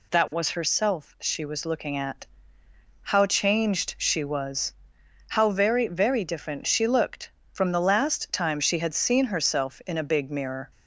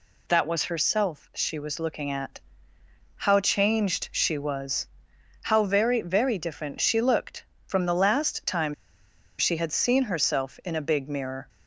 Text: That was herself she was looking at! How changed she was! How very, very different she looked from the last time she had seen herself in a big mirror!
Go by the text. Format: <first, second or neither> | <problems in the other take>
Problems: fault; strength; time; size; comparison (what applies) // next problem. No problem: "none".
first | pauses between "time" and "she"; noticeable; at 8.7 s; 0.64 s long